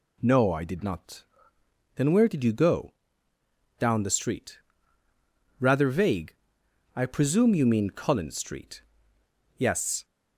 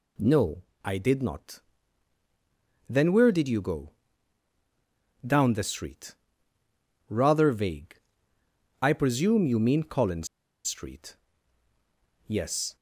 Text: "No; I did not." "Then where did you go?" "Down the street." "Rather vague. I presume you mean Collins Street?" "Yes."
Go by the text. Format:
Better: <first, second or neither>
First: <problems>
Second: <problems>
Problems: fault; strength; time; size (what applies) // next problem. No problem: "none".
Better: first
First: none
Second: pauses between "Collins" and "Street"; at 10.2 s; 0.40 s long